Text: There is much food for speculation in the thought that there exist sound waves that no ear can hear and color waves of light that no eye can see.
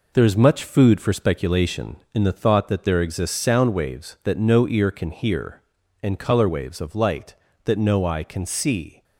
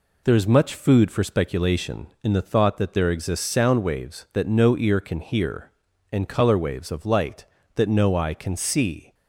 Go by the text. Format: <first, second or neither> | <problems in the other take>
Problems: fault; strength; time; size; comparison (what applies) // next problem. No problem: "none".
second | gets quieter; throughout; 7 dB